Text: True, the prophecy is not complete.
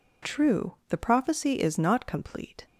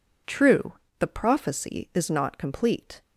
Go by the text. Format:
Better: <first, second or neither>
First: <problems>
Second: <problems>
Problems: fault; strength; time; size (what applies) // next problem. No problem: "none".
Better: neither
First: none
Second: none